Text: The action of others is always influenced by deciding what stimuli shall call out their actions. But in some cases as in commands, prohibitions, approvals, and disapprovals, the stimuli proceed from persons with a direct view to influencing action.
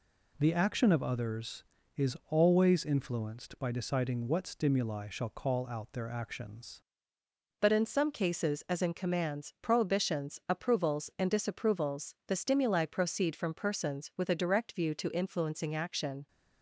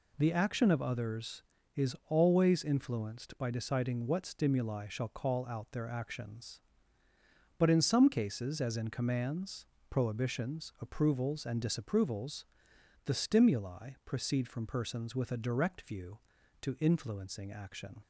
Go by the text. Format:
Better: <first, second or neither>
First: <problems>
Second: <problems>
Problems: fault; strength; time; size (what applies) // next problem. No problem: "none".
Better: second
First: changes voice at "But"; from 7.5 s on; 8.7 s long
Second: none